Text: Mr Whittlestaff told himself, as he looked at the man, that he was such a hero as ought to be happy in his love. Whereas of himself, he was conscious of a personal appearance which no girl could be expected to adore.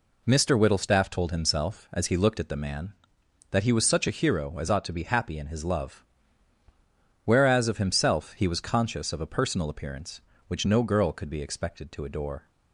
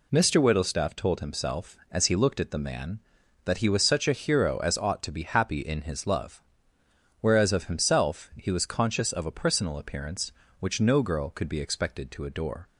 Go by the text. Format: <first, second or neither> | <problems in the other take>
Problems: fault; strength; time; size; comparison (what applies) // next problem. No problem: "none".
neither | none